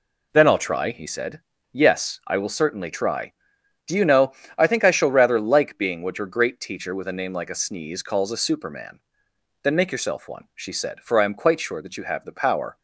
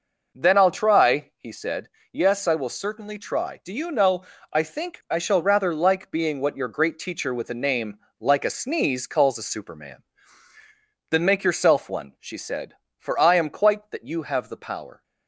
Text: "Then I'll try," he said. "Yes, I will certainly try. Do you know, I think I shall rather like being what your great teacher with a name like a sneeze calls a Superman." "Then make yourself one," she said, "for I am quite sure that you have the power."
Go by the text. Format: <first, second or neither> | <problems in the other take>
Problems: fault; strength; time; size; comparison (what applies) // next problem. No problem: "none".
first | pauses between "name" and "like"; slight; at 7.9 s; 0.22 s long // skips "sure"; at 13.9 s